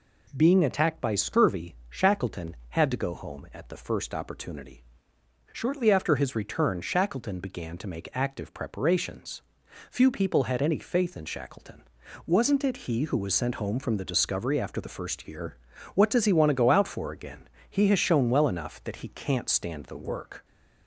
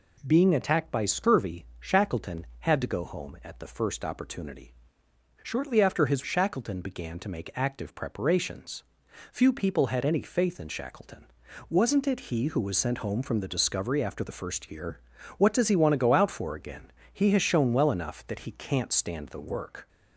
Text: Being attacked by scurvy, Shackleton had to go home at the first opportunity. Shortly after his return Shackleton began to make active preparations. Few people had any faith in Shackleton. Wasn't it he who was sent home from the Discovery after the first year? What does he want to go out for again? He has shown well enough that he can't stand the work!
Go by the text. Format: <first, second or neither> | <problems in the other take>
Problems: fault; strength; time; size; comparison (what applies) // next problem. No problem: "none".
first | skips "return"; at 6.2 s